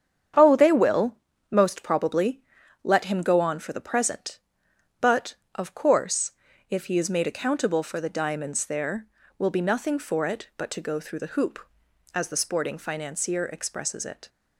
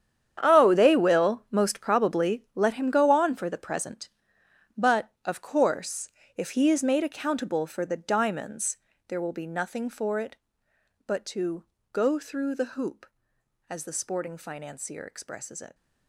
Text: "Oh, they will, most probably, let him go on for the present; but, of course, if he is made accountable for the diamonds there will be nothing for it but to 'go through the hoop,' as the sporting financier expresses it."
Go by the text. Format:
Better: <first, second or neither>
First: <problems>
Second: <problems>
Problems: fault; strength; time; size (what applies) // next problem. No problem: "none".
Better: first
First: starts louder than the rest; strong; until 1.7 s; 8.5 dB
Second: gets quieter; strong; throughout; 15 dB // starts louder than the rest; strong; until 1.4 s; 9 dB // pauses between "diamonds" and "there"; slight; at 8.7 s; 0.32 s long // pauses between "to" and "go"; slight; at 11.6 s; 0.26 s long